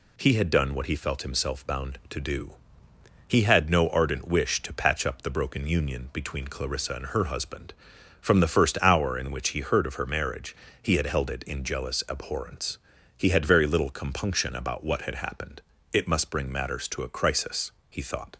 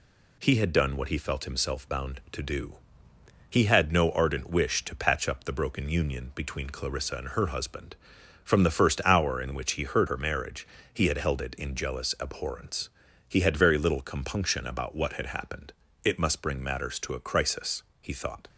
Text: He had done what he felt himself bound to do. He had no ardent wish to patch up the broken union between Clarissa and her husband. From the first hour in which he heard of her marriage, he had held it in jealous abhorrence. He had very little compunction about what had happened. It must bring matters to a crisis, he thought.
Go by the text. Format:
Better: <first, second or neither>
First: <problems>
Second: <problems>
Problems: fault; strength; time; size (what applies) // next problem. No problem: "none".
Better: first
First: none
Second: skips "of"; at 10.0 s